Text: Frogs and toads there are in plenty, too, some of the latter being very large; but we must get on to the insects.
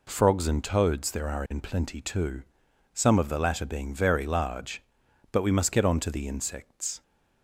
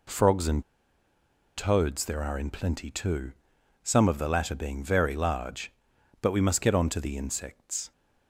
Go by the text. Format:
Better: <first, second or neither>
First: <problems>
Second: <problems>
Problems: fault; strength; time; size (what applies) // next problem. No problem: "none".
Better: first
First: none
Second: pauses between "and" and "toads"; noticeable; at 0.6 s; 0.94 s long